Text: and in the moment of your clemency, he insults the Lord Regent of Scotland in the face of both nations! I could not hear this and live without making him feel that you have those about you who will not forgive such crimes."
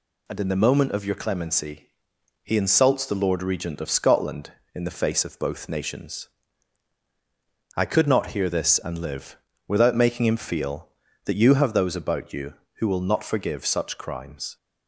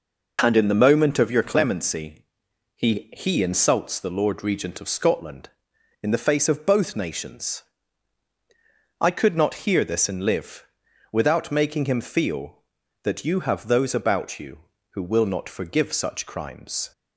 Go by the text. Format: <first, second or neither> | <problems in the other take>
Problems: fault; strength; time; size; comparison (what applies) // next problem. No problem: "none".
first | says "he" twice; at 3.1 s // pauses between "live" and "without"; noticeable; at 10.6 s; 0.48 s long; slight in the first